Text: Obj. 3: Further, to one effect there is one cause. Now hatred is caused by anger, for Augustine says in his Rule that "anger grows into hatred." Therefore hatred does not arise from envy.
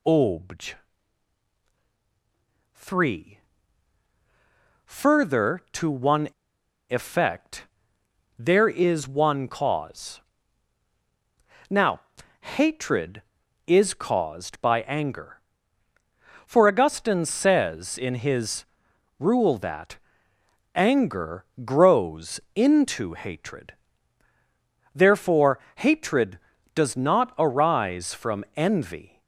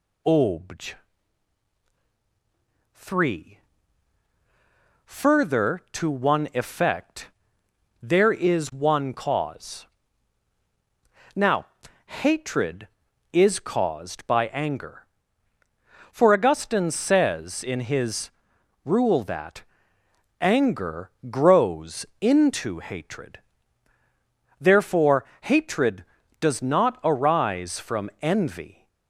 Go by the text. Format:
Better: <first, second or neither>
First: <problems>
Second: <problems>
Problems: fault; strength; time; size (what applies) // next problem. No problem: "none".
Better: second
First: pauses between "one" and "effect"; noticeable; at 6.2 s; 0.60 s long // pauses between "effect" and "there"; noticeable; at 7.6 s; 0.72 s long // pauses between "Now" and "hatred"; at 11.9 s; 0.40 s long // pauses between "his" and "Rule"; noticeable; at 18.6 s; 0.54 s long // pauses between "that" and "anger"; noticeable; at 19.9 s; 0.76 s long // pauses between "anger" and "grows"; slight; at 21.4 s; 0.18 s long // pauses between "Therefore" and "hatred"; slight; at 25.5 s; 0.18 s long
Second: pauses between "effect" and "there"; noticeable; at 7.2 s; 0.72 s long // pauses between "Now" and "hatred"; at 11.6 s; 0.40 s long // pauses between "his" and "Rule"; noticeable; at 18.2 s; 0.54 s long // pauses between "that" and "anger"; noticeable; at 19.6 s; 0.76 s long // pauses between "anger" and "grows"; slight; at 21.1 s; 0.18 s long // pauses between "Therefore" and "hatred"; slight; at 25.2 s; 0.18 s long